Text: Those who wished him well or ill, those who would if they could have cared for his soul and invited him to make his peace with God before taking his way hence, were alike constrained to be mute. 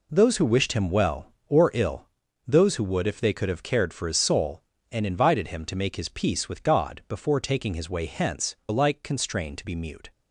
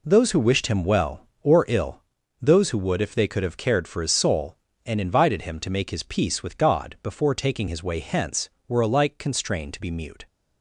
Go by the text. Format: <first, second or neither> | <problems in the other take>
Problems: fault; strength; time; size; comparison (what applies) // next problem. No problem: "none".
second | skips "were"; at 8.6 s